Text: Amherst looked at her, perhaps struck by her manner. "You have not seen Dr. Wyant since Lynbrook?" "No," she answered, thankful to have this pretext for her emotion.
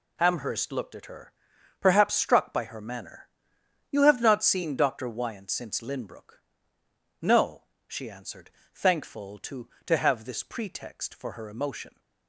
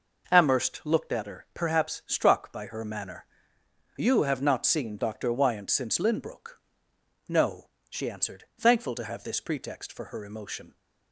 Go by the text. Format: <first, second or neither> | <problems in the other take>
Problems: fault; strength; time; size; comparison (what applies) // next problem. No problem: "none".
second | says "to" twice; at 9.8 s